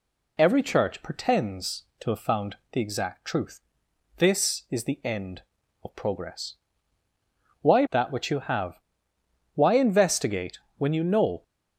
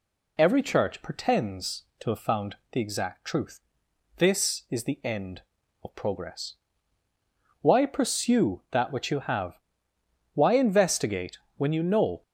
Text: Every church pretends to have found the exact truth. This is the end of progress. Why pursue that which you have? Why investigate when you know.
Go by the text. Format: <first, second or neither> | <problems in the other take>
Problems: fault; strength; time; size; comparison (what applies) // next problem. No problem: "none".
second | skips "pursue"; at 7.8 s // pauses between "investigate" and "when"; slight; at 10.5 s; 0.20 s long; slight in the second